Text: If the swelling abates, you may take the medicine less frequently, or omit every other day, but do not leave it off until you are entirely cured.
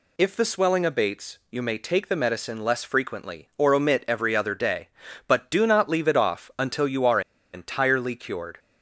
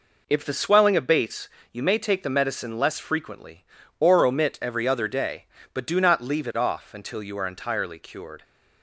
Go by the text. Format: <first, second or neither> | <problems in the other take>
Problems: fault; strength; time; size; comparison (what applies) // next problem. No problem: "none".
second | pauses between "are" and "entirely"; slight; at 7.1 s; 0.33 s long